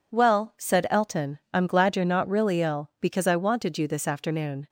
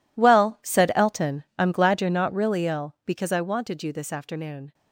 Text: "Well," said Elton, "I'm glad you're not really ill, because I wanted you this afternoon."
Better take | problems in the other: first | gets quieter; strong; throughout; 15 dB

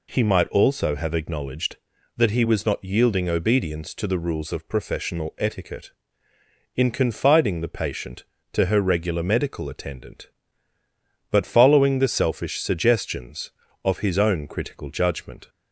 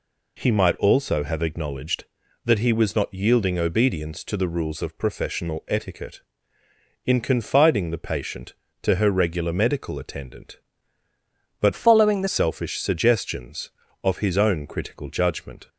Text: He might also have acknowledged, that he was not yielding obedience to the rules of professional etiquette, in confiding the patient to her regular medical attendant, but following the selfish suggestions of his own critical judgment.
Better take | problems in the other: first | changes voice from "following" to "the"; from 11.7 to 12.2 s; 0.5 s long

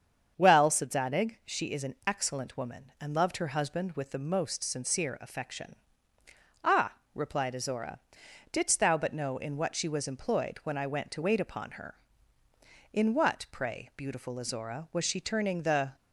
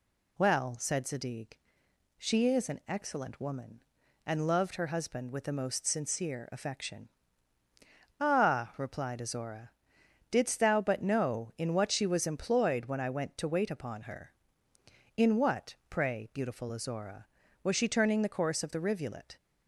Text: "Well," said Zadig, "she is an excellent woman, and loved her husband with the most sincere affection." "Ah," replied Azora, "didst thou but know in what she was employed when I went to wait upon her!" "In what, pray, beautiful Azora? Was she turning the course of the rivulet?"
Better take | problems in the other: second | starts louder than the rest; strong; until 1.3 s; 7.5 dB // stops before "course of the rivulet"; at 15.9 s

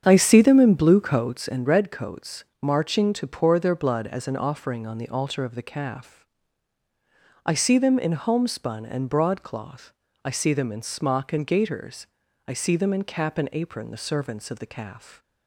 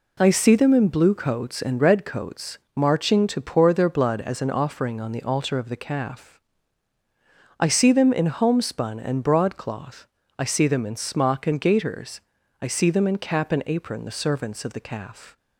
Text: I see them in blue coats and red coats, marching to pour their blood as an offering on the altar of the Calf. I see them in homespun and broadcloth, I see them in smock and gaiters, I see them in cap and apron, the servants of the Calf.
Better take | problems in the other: second | starts louder than the rest; strong; until 1.5 s; 8 dB

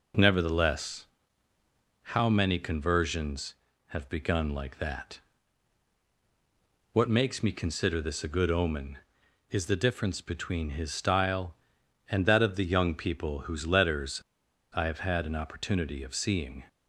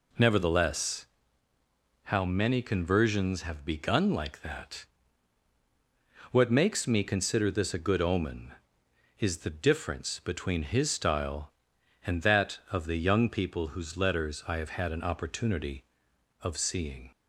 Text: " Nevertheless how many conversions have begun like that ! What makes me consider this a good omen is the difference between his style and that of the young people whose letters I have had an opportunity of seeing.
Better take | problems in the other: second | pauses between "Nevertheless" and "how"; noticeable; at 1.0 s; 0.94 s long; also in the second // pauses between "letters" and "I"; noticeable; at 14.2 s; 0.51 s long

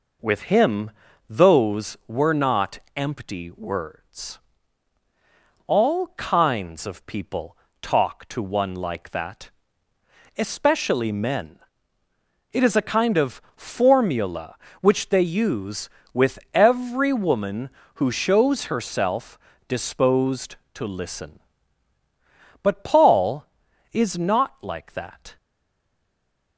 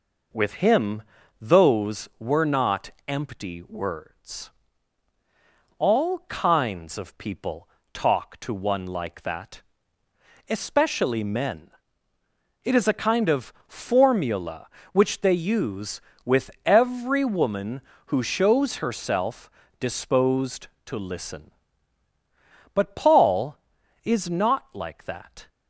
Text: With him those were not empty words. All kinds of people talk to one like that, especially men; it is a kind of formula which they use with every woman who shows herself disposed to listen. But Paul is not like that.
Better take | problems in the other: second | pauses between "him" and "those"; at 0.9 s; 0.38 s long; also in the second // pauses between "not" and "empty"; slight; at 2.7 s; 0.16 s long; slight in the second // pauses between "people" and "talk"; slight; at 7.5 s; 0.24 s long; slight in the second // pauses between "of" and "formula"; slight; at 13.4 s; 0.16 s long; slight in the second // pauses between "herself" and "disposed"; slight; at 19.3 s; 0.28 s long; slight in the second // stays silent after the last word; noticeable; from 25.3 s on; 1.2 s long

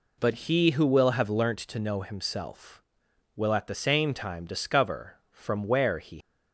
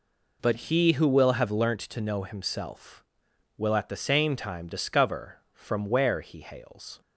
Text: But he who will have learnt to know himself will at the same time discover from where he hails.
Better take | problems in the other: second | stops before "hails"; at 6.2 s

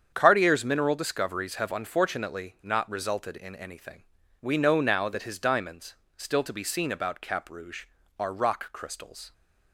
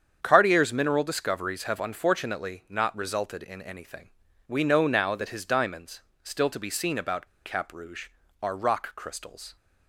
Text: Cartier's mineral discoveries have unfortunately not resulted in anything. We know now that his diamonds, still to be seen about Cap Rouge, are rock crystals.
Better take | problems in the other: first | starts louder than the rest; strong; until 1.2 s; 8 dB; strong in the first // pauses between "about" and "Cap"; slight; at 7.2 s; 0.17 s long

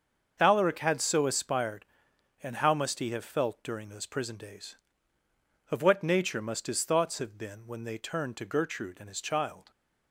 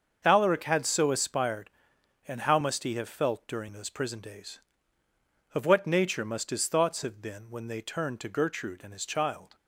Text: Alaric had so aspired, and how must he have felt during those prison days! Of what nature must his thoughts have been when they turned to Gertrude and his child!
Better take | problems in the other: neither | starts louder than the rest; the same in both

